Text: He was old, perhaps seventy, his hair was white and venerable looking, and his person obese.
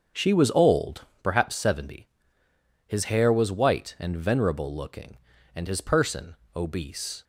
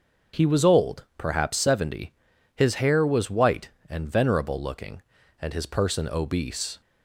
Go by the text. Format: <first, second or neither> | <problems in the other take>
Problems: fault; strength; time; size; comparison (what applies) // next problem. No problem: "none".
second | starts louder than the rest; until 1.3 s; 6.5 dB; also in the second // says "She" for "He"; at 0.1 s // pauses between "person" and "obese"; slight; at 6.3 s; 0.20 s long